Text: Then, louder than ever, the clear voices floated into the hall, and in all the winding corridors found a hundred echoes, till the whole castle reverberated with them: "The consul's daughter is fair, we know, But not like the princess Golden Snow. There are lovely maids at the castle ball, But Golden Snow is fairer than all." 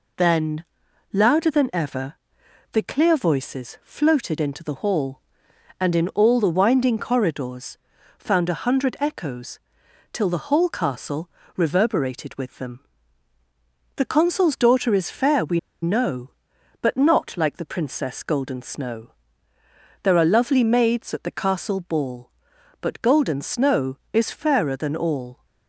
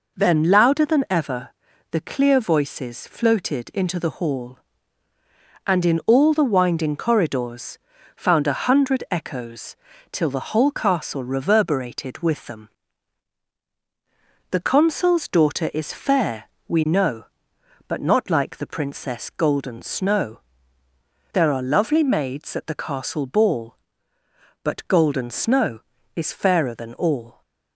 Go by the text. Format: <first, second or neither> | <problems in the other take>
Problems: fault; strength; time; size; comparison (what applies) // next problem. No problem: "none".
second | pauses between "corridors" and "found"; at 7.7 s; 0.42 s long; also in the second // pauses between "castle" and "reverberated"; slight; at 11.2 s; 0.28 s long // pauses between "we" and "know"; slight; at 15.5 s; 0.23 s long